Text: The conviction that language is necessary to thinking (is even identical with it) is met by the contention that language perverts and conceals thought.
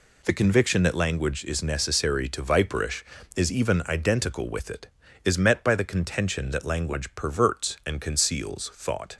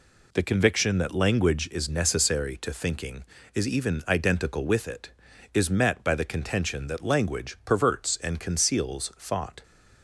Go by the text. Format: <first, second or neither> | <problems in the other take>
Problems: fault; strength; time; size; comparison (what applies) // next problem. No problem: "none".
second | says "viperish" for "thinking"; at 2.4 s